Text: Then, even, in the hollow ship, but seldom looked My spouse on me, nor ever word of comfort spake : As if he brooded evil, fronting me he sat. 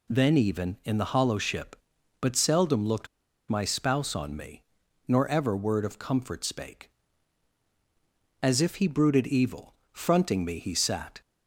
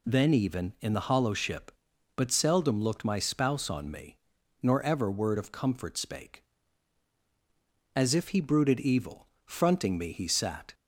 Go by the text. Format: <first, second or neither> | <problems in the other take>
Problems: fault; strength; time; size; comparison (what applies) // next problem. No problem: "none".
second | pauses between "looked" and "My"; at 3.0 s; 0.43 s long